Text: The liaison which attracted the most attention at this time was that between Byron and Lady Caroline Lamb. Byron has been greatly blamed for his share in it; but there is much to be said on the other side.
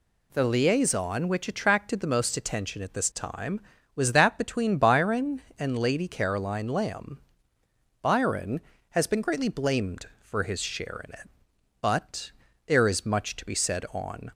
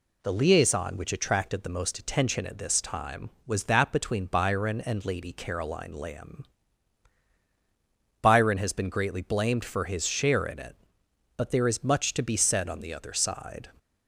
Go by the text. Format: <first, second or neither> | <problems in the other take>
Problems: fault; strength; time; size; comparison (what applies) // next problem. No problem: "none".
second | pauses between "but" and "there"; slight; at 12.3 s; 0.34 s long // stops before "the other side"; at 14.2 s